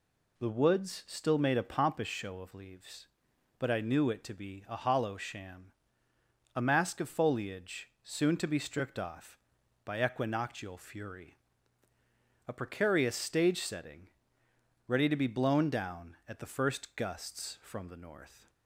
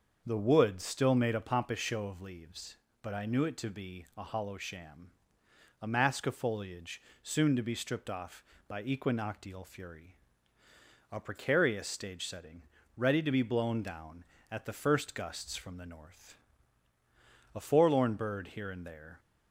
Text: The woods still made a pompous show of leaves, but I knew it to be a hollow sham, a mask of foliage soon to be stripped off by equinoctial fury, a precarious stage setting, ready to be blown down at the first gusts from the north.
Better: first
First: pauses between "foliage" and "soon"; slight; at 7.8 s; 0.16 s long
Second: starts louder than the rest; until 1.2 s; 6.5 dB // pauses between "foliage" and "soon"; slight; at 7.0 s; 0.22 s long // goes on to say "A forlorn bird here and there"; from 17.5 s on; 1.6 s long

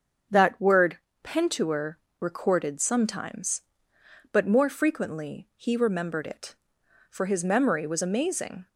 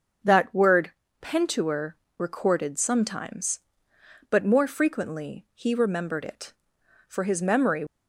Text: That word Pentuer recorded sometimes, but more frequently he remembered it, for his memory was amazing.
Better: first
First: starts louder than the rest; until 1.5 s; 7 dB // pauses between "word" and "Pentuer"; slight; at 0.9 s; 0.26 s long // pauses between "Pentuer" and "recorded"; slight; at 1.9 s; 0.22 s long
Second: starts louder than the rest; until 1.5 s; 6.5 dB // pauses between "word" and "Pentuer"; slight; at 0.9 s; 0.30 s long // pauses between "Pentuer" and "recorded"; slight; at 1.9 s; 0.22 s long // stops before "was amazing"; at 7.8 s

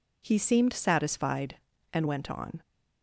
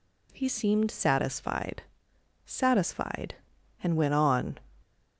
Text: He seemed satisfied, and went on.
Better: first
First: none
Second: says "satisfied" twice; at 2.4 s

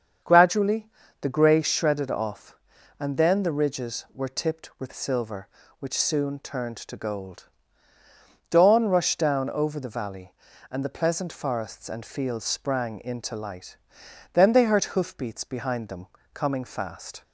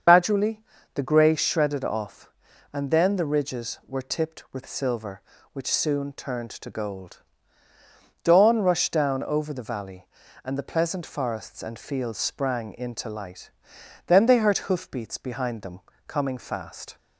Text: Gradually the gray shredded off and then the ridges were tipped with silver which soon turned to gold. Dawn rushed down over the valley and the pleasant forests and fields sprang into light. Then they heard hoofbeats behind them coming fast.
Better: first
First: starts louder than the rest; strong; until 1.5 s; 7.5 dB // pauses between "Gradually" and "the"; slight; at 0.8 s; 0.34 s long // pauses between "them" and "coming"; slight; at 16.0 s; 0.28 s long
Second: loses the start of "Gradually"; at 0.0 s; 95 ms // starts louder than the rest; until 1.4 s; 7 dB // pauses between "Gradually" and "the"; slight; at 0.5 s; 0.34 s long // pauses between "them" and "coming"; slight; at 15.7 s; 0.28 s long

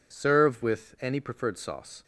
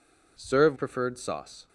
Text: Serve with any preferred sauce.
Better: first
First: none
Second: skips "with any"; at 0.7 s

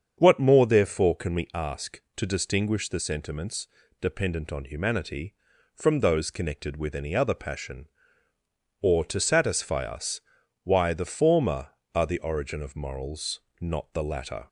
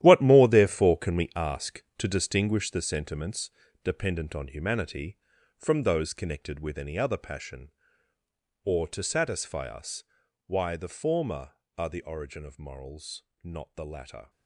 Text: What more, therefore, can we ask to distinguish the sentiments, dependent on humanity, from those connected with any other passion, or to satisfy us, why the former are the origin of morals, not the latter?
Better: first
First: starts louder than the rest; strong; until 1.1 s; 7.5 dB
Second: gets quieter; strong; throughout; 12.5 dB // starts louder than the rest; strong; until 1.0 s; 12.5 dB

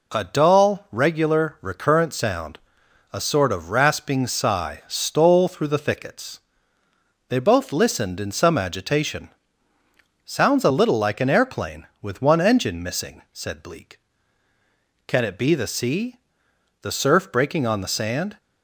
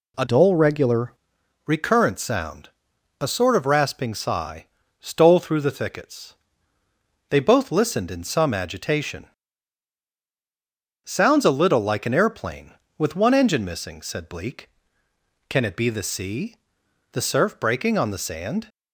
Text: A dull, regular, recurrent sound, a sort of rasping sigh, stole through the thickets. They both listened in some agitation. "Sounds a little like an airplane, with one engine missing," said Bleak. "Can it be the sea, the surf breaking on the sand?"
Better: first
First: none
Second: changes voice from "dull" to "regular"; from 0.2 to 1.1 s; 0.9 s long

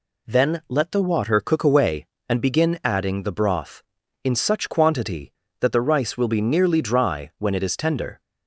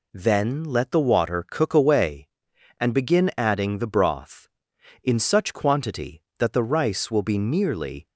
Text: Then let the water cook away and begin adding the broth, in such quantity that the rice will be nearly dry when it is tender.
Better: first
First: none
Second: stops before "dry when it is tender"; at 8.0 s

